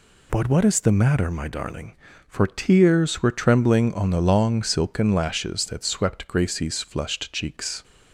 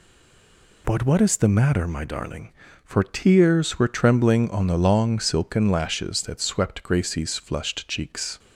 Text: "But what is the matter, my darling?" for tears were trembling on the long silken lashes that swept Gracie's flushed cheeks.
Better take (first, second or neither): first